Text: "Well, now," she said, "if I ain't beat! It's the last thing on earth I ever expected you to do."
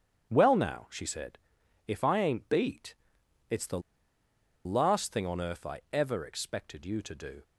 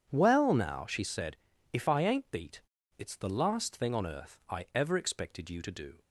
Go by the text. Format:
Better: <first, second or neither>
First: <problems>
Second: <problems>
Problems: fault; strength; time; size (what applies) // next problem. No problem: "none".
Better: second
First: starts louder than the rest; strong; until 1.3 s; 9 dB // pauses between "the" and "last"; noticeable; at 3.7 s; 0.85 s long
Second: starts louder than the rest; strong; until 1.1 s; 8 dB